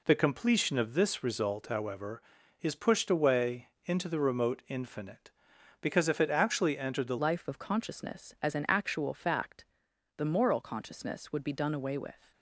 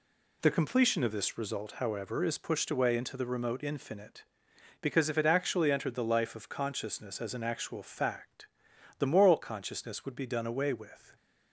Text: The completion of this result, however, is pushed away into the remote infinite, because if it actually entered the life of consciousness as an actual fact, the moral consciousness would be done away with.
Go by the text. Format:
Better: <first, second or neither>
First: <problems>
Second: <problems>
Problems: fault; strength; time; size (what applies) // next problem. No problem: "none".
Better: second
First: pauses between "away" and "into"; slight; at 3.6 s; 0.16 s long // changes voice at "life"; from 7.2 s on; 5.1 s long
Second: none